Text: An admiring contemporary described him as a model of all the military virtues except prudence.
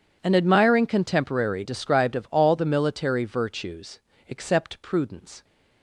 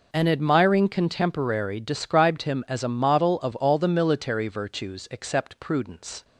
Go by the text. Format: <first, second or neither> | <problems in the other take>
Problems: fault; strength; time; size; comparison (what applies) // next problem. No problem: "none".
second | skips "him as a model"; at 2.1 s // pauses between "virtues" and "except"; slight; at 3.9 s; 0.28 s long